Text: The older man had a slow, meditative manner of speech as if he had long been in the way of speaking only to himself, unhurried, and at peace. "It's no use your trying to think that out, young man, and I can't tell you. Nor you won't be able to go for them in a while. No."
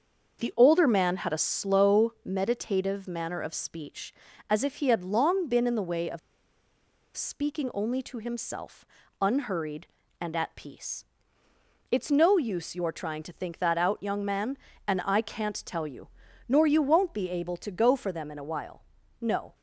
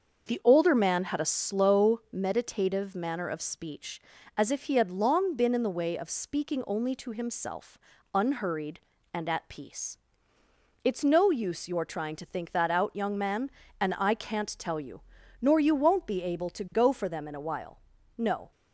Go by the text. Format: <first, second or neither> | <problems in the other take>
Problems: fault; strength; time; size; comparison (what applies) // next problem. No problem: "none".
second | starts louder than the rest; until 1.4 s; 6.5 dB; also in the second // pauses between "of" and "speaking"; noticeable; at 6.1 s; 0.96 s long